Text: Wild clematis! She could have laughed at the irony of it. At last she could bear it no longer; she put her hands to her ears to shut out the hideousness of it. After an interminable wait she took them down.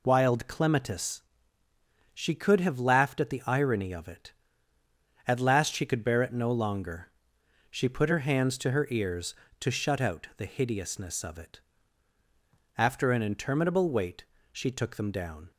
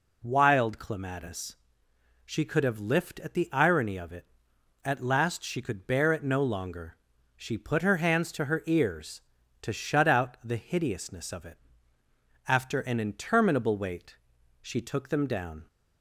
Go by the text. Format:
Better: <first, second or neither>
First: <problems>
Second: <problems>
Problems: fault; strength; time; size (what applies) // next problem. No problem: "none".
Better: first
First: pauses between "wait" and "she"; slight; at 14.2 s; 0.26 s long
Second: says "lift" for "laughed"; at 2.7 s // pauses between "wait" and "she"; noticeable; at 14.1 s; 0.46 s long